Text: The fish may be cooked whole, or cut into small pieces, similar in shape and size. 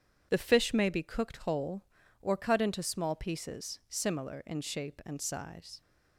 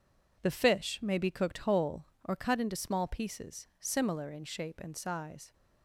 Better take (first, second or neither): neither